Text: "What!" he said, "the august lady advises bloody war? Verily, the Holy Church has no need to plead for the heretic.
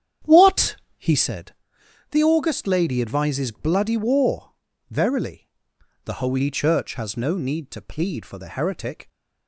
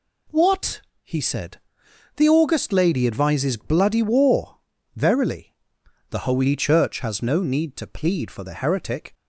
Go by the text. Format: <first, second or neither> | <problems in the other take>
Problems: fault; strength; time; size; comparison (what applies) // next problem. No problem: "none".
second | starts louder than the rest; strong; until 1.3 s; 9 dB